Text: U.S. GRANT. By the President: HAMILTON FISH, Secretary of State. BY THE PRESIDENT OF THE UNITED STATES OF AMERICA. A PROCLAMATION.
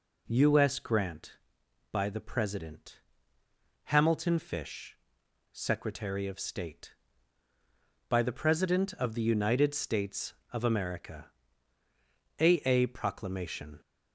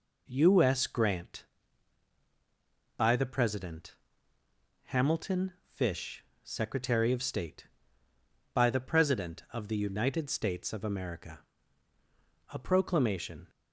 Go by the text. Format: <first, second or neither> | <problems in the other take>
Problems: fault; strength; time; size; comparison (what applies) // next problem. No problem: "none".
second | says "A" twice; at 12.6 s